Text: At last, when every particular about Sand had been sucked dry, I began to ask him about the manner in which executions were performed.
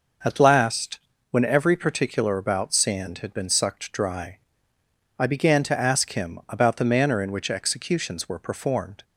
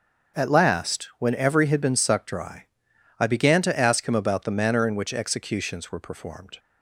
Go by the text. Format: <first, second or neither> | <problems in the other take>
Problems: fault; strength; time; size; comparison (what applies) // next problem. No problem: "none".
first | starts louder than the rest; until 1.4 s; 6.5 dB // skips "particular about Sand"; at 1.6 s